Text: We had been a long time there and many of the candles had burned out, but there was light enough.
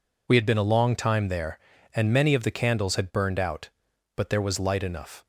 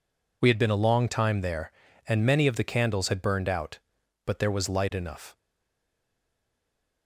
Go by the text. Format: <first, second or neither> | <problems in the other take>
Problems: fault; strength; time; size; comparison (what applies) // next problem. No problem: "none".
first | stays silent after the last word; noticeable; from 5.3 s on; 1.7 s long